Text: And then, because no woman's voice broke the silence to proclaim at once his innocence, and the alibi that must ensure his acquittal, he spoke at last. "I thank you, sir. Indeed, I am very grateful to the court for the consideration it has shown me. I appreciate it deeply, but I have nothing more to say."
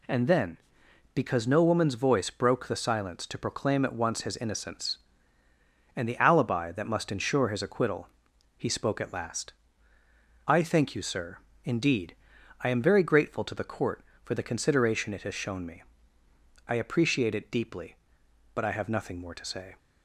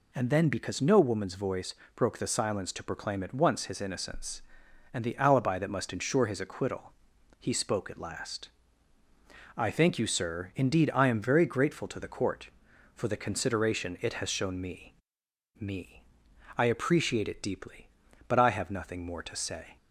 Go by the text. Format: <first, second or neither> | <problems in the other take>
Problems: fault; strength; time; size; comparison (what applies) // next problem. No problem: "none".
first | pauses between "voice" and "broke"; slight; at 1.7 s; 0.20 s long // says "me" twice; at 15.6 s